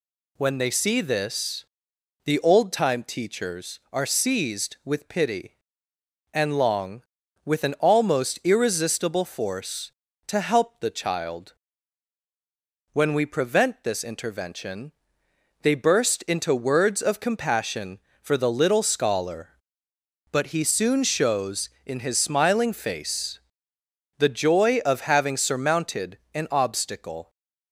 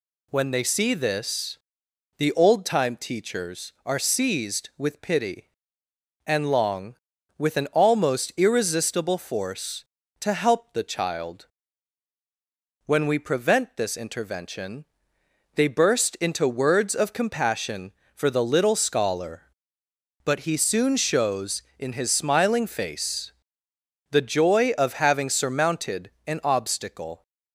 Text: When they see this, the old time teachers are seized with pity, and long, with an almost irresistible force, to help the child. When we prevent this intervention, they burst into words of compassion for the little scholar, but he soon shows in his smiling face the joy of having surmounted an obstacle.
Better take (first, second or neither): neither